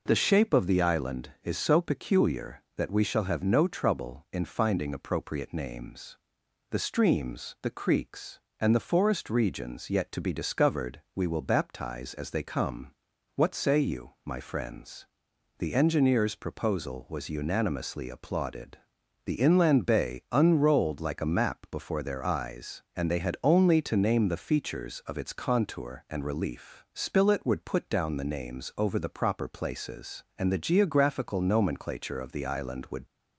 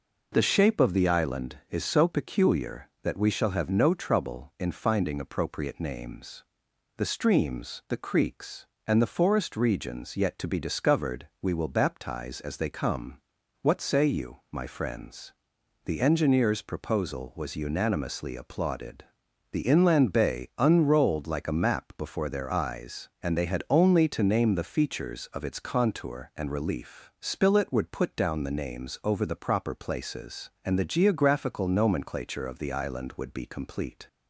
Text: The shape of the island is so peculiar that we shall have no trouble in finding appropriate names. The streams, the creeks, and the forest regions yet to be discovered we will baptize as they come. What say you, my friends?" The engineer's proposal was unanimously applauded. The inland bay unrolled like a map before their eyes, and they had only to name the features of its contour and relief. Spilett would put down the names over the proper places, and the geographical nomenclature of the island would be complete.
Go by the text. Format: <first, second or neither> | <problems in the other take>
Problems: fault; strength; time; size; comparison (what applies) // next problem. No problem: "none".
second | pauses between "discovered" and "we"; slight; at 11.0 s; 0.16 s long; slight in the second // stops before "be complete"; at 33.0 s